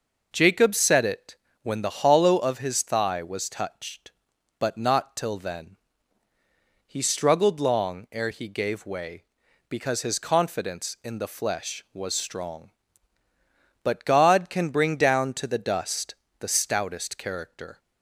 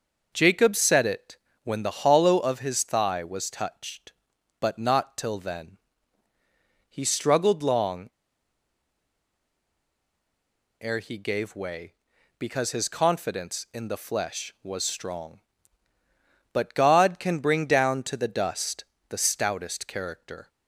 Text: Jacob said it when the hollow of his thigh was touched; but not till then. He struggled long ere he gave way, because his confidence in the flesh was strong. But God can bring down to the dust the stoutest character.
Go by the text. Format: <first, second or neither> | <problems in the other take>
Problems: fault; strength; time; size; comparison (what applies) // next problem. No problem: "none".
first | pauses between "it" and "when"; slight; at 1.3 s; 0.26 s long; slight in the first // pauses between "long" and "ere"; strong; at 8.0 s; 2.7 s long // pauses between "dust" and "the"; slight; at 18.8 s; 0.28 s long; slight in the first